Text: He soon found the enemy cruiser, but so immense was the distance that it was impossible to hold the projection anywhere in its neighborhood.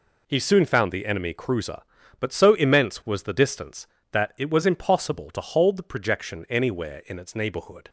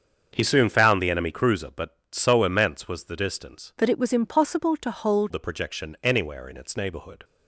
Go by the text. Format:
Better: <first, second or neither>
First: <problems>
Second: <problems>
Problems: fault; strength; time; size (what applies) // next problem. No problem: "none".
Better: first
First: none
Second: starts louder than the rest; until 1.3 s; 7 dB // changes voice from "that" to "hold"; from 3.7 to 5.3 s; 1.6 s long